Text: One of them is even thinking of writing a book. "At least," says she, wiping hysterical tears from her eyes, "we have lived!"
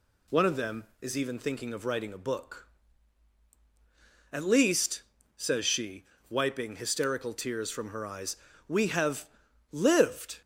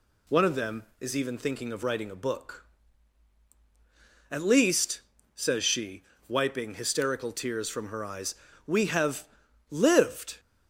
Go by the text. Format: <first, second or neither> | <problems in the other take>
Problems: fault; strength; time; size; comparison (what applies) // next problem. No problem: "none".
neither | pauses between "have" and "lived"; the same in both